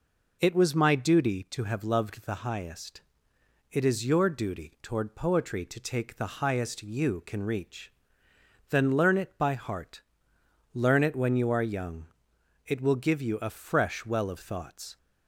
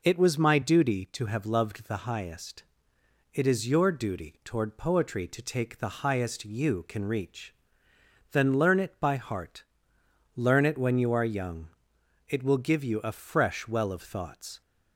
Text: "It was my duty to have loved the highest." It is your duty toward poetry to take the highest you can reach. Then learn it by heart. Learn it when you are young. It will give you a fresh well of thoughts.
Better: neither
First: none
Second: none

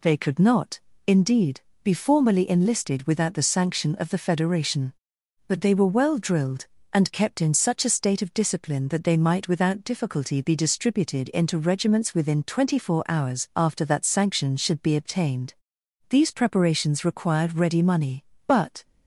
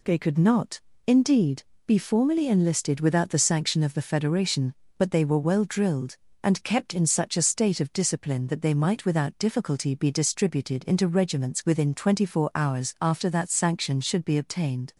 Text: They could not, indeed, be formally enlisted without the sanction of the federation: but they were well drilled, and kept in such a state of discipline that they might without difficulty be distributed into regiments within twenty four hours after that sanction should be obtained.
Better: second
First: goes on to say "These preparations required ready money but"; strong; from 16.0 s on; 2.7 s long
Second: none

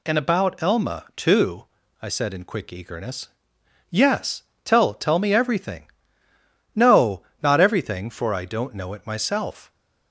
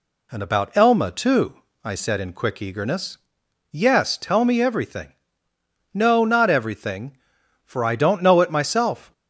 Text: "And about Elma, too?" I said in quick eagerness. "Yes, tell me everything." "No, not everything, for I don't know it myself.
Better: second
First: says "tell" twice; at 4.9 s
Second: none

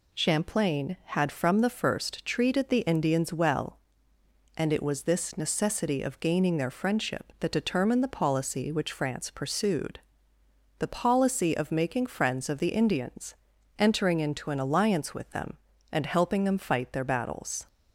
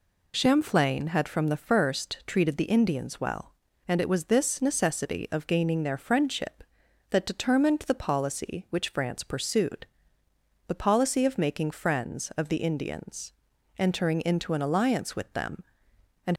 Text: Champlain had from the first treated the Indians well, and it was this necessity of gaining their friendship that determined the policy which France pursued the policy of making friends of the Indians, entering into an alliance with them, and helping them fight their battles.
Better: first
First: pauses between "pursued" and "the"; noticeable; at 9.9 s; 0.80 s long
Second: pauses between "pursued" and "the"; noticeable; at 9.8 s; 0.80 s long // stops before "helping them fight their battles"; at 16.3 s

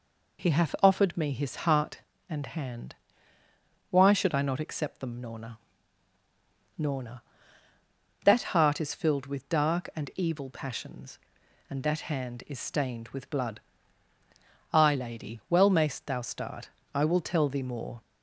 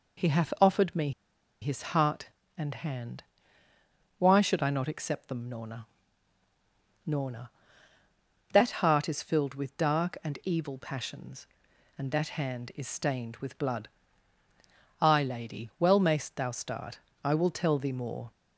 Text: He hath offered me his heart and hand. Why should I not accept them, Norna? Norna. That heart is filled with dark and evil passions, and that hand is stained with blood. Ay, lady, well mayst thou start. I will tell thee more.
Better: first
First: none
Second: pauses between "me" and "his"; noticeable; at 1.1 s; 0.51 s long

